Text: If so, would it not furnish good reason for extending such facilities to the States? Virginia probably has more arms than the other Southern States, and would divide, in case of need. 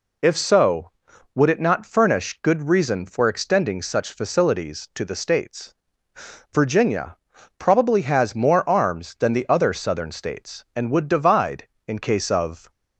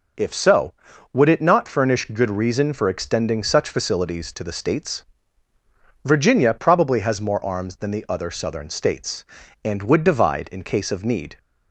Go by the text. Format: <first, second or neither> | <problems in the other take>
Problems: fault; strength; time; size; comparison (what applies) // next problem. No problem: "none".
second | pauses between "Virginia" and "probably"; at 7.1 s; 0.40 s long // stops before "need"; at 12.6 s